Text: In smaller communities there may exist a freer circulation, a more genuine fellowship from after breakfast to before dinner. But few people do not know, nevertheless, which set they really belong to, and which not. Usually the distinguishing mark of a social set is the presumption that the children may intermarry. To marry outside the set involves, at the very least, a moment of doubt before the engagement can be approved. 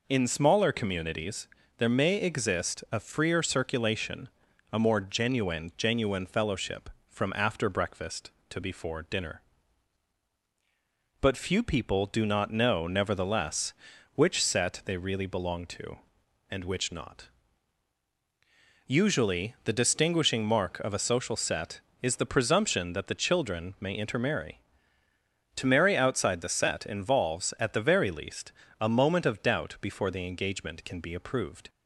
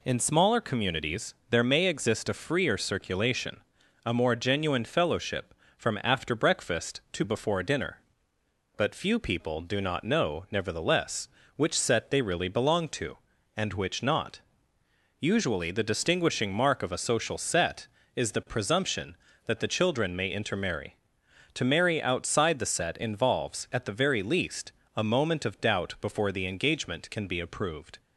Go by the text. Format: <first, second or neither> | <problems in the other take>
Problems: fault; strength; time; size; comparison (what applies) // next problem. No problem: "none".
second | pauses between "communities" and "there"; slight; at 1.4 s; 0.30 s long; slight in the second // says "genuine" twice; at 5.7 s